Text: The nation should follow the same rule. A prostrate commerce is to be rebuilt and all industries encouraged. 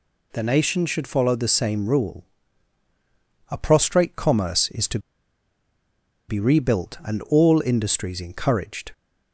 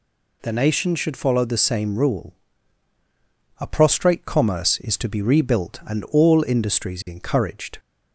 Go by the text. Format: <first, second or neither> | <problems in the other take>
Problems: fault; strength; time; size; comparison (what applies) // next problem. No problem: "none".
second | pauses between "to" and "be"; strong; at 4.9 s; 1.3 s long